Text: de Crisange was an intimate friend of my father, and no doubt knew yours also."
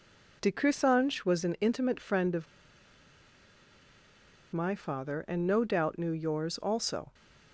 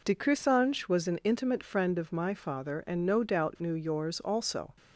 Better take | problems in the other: second | pauses between "of" and "my"; strong; at 2.4 s; 2.0 s long

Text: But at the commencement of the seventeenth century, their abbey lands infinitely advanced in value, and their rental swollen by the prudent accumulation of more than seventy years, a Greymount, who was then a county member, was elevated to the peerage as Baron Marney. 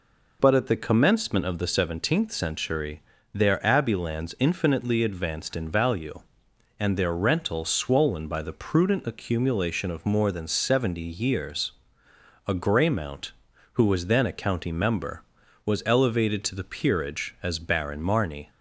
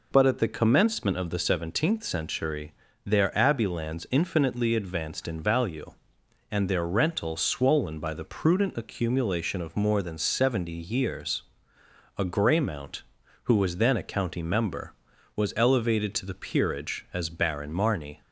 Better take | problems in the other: neither | none

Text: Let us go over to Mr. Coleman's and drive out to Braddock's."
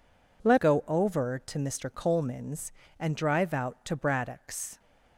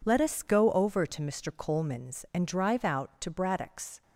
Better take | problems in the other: second | skips "us"; at 0.5 s

